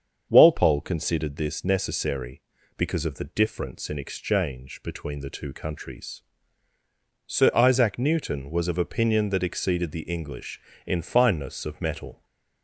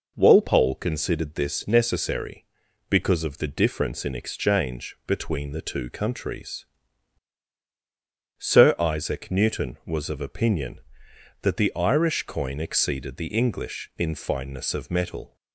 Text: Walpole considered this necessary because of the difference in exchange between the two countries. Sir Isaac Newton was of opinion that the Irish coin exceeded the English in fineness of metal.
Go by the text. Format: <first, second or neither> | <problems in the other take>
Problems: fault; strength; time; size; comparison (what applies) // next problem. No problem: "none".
second | starts louder than the rest; until 1.3 s; 7 dB // skips "the Irish coin"; at 9.4 s